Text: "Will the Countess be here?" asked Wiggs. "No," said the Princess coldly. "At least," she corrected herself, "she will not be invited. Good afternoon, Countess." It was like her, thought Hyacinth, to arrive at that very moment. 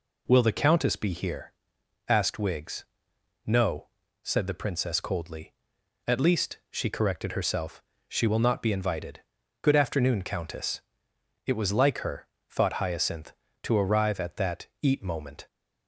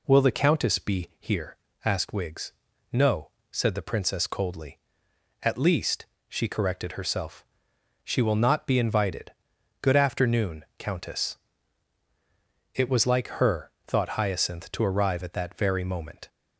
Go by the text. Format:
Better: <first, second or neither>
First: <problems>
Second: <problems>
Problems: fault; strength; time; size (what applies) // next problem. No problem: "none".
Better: second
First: says "eat" for "very"; at 14.8 s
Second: none